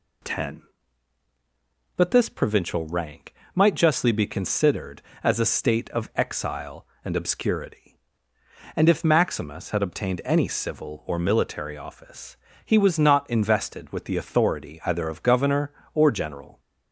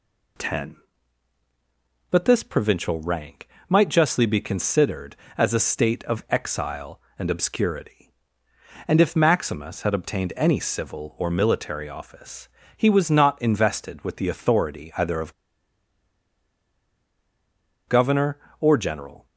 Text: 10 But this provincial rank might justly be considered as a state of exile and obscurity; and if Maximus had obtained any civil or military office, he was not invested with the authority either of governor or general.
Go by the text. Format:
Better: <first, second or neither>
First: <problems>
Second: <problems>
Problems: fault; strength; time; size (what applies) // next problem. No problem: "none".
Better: first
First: pauses between "rank" and "might"; slight; at 3.3 s; 0.22 s long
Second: pauses between "rank" and "might"; slight; at 3.4 s; 0.22 s long // pauses between "of" and "governor"; strong; at 15.3 s; 2.5 s long